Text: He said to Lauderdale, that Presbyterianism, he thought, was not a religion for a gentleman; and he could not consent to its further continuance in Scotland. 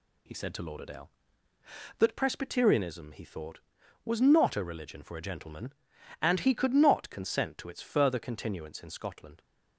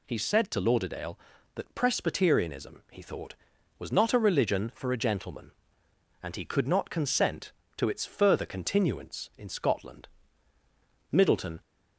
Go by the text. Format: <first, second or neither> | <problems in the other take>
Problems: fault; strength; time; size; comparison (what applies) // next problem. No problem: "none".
first | goes on to say "Middleton"; from 11.1 s on; 0.50 s long